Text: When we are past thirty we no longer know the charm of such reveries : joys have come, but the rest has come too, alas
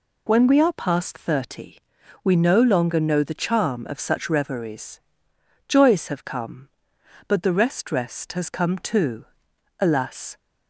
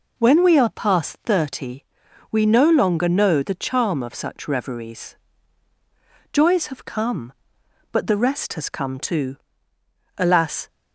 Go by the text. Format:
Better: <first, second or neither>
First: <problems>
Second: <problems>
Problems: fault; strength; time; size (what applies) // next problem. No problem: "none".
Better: second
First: pauses between "thirty" and "we"; at 1.7 s; 0.44 s long // says "rest" twice; at 7.9 s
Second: pauses between "thirty" and "we"; noticeable; at 1.8 s; 0.48 s long